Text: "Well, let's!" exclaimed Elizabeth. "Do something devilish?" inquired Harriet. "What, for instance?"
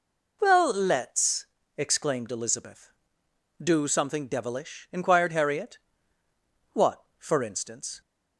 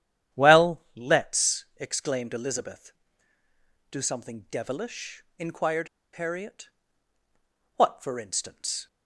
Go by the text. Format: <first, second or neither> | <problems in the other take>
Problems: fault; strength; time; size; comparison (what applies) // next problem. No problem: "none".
first | starts louder than the rest; strong; until 1.4 s; 10.5 dB // pauses between "inquired" and "Harriet"; slight; at 5.8 s; 0.26 s long